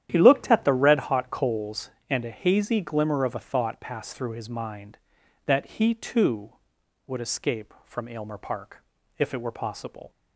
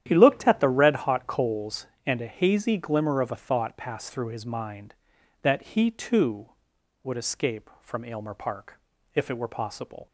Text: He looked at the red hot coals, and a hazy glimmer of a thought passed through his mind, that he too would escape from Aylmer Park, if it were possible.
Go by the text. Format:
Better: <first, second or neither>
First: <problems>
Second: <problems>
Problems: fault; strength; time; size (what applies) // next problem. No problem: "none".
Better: neither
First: starts louder than the rest; strong; until 1.1 s; 11 dB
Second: starts louder than the rest; strong; until 1.0 s; 11 dB